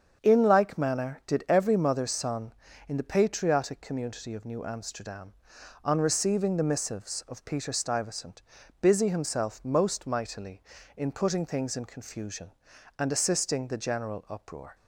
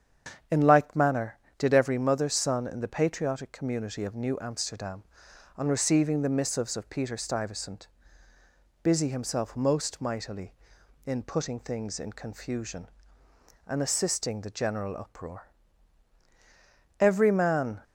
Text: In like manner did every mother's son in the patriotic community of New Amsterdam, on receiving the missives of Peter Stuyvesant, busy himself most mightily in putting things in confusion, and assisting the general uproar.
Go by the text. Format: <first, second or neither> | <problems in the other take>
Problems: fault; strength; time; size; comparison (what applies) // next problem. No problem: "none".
first | starts louder than the rest; strong; until 1.7 s; 8 dB; strong in the first // goes on to say "Every man"; noticeable; from 16.9 s on; 0.84 s long